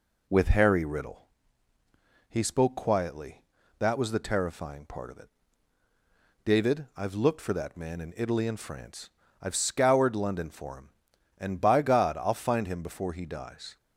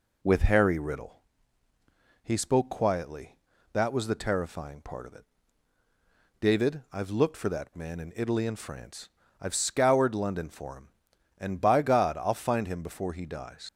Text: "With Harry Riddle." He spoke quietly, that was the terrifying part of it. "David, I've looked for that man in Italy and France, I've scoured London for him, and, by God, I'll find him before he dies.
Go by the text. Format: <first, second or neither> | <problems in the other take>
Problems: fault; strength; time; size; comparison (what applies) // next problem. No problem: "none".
first | leaves "dies" unfinished; at 13.6 s; 75 ms